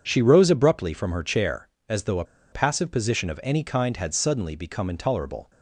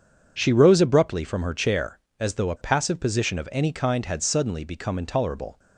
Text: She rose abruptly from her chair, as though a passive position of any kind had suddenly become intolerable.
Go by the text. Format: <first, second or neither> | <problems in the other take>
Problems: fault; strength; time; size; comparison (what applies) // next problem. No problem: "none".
second | pauses between "a" and "passive"; slight; at 2.2 s; 0.28 s long